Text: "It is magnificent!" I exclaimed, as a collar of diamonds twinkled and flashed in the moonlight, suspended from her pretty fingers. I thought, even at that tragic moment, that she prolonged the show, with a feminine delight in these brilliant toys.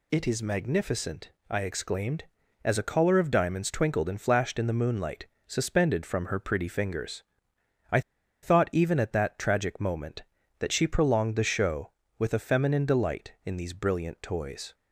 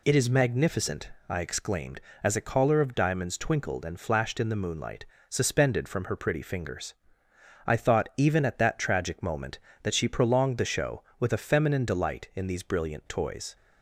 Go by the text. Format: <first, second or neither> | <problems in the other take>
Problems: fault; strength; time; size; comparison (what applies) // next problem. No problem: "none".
second | pauses between "I" and "thought"; at 7.9 s; 0.42 s long